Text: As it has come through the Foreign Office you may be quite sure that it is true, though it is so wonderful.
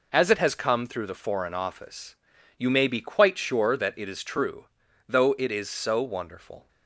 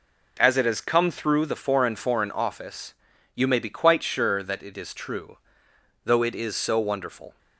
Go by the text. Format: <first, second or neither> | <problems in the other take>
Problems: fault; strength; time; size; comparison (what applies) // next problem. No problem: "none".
first | says "Foreign" twice; at 1.9 s // pauses between "Office" and "you"; at 2.9 s; 0.40 s long; also in the first